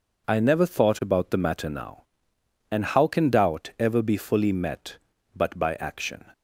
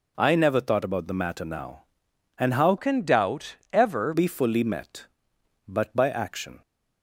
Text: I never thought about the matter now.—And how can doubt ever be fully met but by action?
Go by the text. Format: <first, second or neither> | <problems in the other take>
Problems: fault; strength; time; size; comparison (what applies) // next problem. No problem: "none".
first | changes voice from "can" to "ever"; from 2.7 to 4.1 s; 1.4 s long // pauses between "doubt" and "ever"; slight; at 3.5 s; 0.18 s long